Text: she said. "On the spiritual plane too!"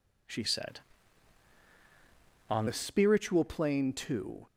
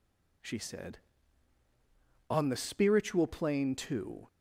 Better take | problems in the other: second | changes voice from "said" to "On"; from 0.4 to 2.6 s; 2.2 s long

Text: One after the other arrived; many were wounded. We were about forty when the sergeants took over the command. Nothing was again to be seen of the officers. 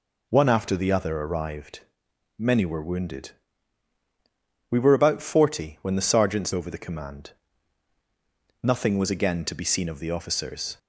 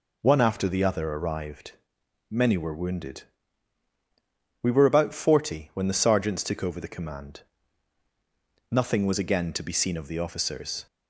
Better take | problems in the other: second | skips "took"; at 6.5 s

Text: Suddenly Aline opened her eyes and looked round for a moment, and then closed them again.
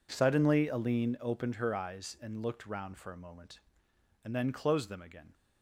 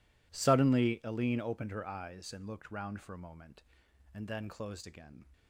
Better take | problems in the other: first | skips "them"; at 4.8 s

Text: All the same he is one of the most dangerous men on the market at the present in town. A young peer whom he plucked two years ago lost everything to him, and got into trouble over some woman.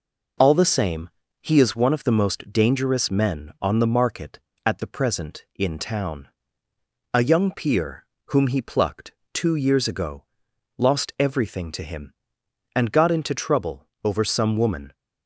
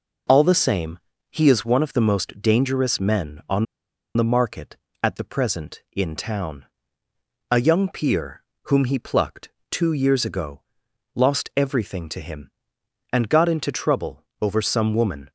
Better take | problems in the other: first | pauses between "same" and "he"; slight; at 0.9 s; 0.30 s long; slight in the first // pauses between "on" and "the"; noticeable; at 3.6 s; 0.51 s long // pauses between "peer" and "whom"; slight; at 8.4 s; 0.22 s long; slight in the first // pauses between "plucked" and "two"; slight; at 9.4 s; 0.22 s long; slight in the first // pauses between "ago" and "lost"; noticeable; at 10.6 s; 0.54 s long; noticeable in the first // pauses between "trouble" and "over"; slight; at 14.2 s; 0.16 s long; slight in the first

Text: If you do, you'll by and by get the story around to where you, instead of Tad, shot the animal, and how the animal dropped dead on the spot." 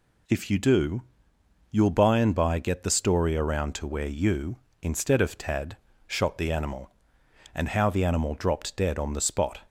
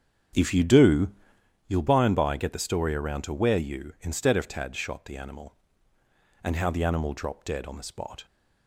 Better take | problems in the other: first | starts louder than the rest; strong; until 1.5 s; 8 dB

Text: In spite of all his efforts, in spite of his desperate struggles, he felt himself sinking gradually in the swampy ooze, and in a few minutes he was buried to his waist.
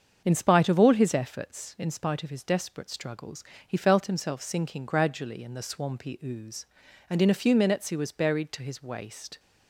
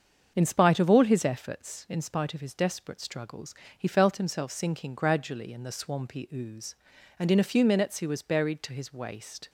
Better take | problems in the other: neither | starts louder than the rest; the same in both

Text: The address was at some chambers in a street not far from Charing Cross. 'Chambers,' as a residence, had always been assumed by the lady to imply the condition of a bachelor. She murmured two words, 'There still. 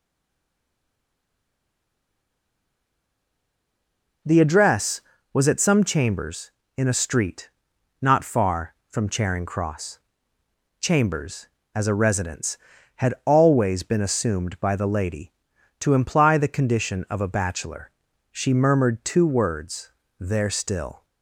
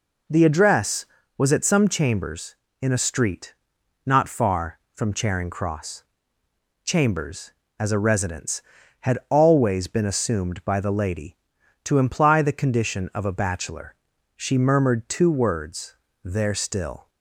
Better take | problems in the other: second | stays silent before the first word; strong; until 4.2 s; 4.2 s long // pauses between "street" and "not"; noticeable; at 7.4 s; 0.54 s long; noticeable in the second

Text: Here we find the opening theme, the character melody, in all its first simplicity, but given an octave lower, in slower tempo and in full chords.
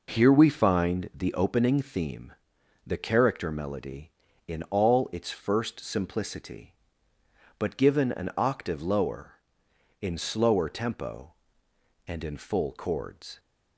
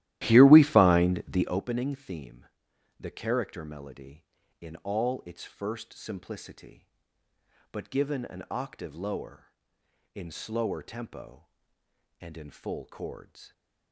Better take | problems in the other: first | starts louder than the rest; strong; until 1.6 s; 14.5 dB

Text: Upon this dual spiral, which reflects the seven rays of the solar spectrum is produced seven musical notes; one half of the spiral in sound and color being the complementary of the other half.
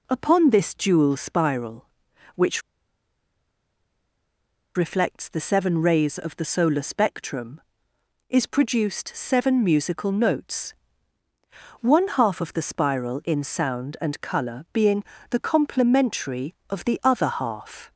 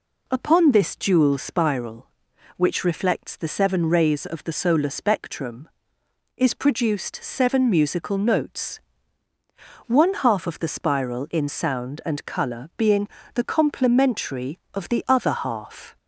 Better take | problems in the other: second | pauses between "which" and "reflects"; strong; at 2.6 s; 2.1 s long // pauses between "being" and "the"; slight; at 15.0 s; 0.26 s long; slight in the second

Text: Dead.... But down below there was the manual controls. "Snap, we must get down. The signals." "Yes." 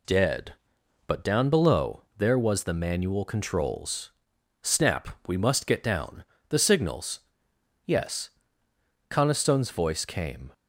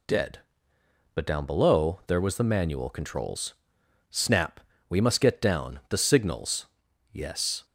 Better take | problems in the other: second | goes on to say "Coniston's voice came"; from 9.1 s on; 1.4 s long

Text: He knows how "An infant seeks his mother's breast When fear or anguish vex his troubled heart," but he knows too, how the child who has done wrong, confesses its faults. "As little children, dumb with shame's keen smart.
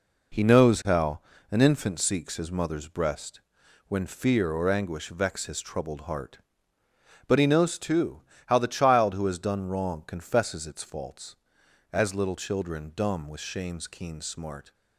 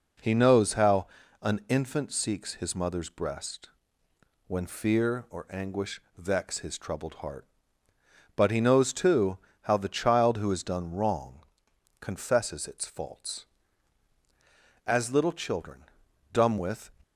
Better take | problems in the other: first | pauses between "how" and "An"; slight; at 1.0 s; 0.34 s long; slight in the first // pauses between "breast" and "When"; noticeable; at 3.6 s; 0.78 s long; noticeable in the first // pauses between "anguish" and "vex"; slight; at 6.0 s; 0.16 s long // stops before "shame's keen smart"; at 17.0 s

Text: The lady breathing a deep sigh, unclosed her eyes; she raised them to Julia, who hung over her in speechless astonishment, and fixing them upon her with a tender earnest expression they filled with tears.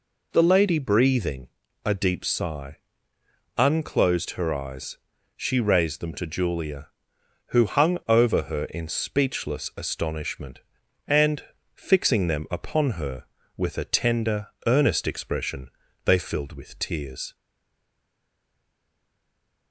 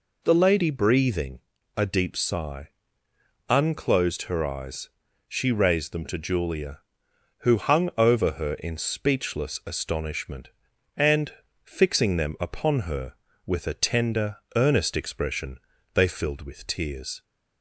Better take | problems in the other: second | pauses between "breathing" and "a"; slight; at 1.4 s; 0.36 s long; slight in the second // pauses between "and" and "fixing"; slight; at 11.4 s; 0.32 s long; slight in the second // pauses between "tender" and "earnest"; slight; at 14.4 s; 0.18 s long; slight in the second // pauses between "expression" and "they"; slight; at 15.6 s; 0.36 s long; slight in the second // stays silent after the last word; from 17.3 s on; 2.4 s long

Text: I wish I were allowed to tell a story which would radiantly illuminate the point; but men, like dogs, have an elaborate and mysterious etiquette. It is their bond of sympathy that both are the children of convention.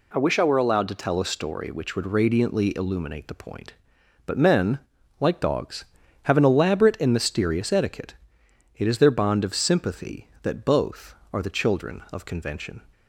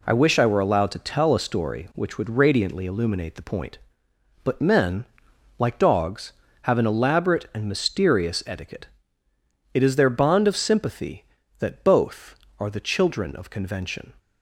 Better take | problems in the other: neither | none

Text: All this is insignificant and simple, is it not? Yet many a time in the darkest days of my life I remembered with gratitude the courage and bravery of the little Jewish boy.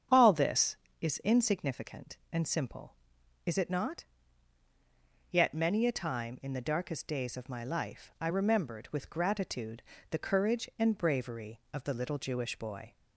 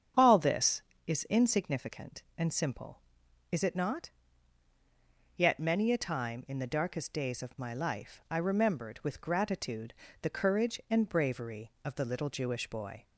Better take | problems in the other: neither | starts louder than the rest; strong; the same in both // pauses between "gratitude" and "the"; slight; the same in both

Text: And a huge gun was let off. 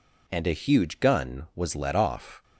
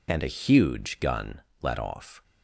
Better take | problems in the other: first | skips "was"; at 1.5 s

